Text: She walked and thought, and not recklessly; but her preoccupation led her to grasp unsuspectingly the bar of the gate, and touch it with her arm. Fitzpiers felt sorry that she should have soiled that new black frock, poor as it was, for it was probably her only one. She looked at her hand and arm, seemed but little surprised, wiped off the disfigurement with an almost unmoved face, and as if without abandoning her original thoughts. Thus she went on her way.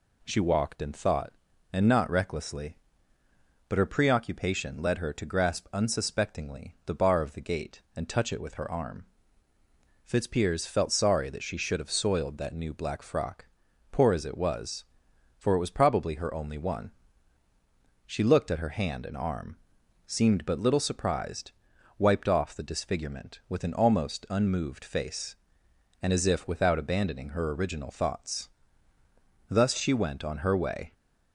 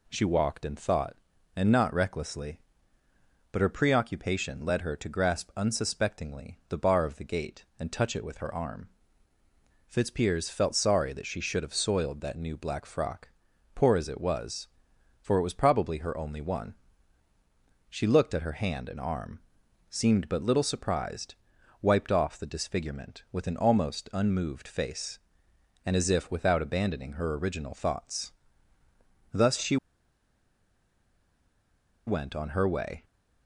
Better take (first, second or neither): first